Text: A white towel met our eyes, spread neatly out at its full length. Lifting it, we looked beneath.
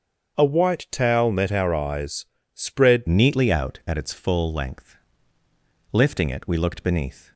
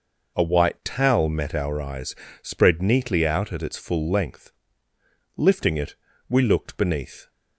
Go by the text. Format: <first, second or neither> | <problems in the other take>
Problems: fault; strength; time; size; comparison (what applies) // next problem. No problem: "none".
second | starts louder than the rest; until 1.4 s; 7 dB // changes voice at "neatly"; from 3.0 s on; 4.3 s long